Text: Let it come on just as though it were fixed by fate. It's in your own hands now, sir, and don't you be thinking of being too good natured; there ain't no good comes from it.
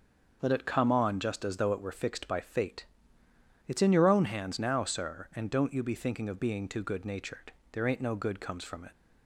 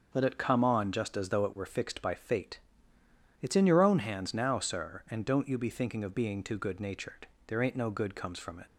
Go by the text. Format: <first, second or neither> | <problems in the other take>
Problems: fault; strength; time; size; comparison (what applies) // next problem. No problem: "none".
neither | starts louder than the rest; the same in both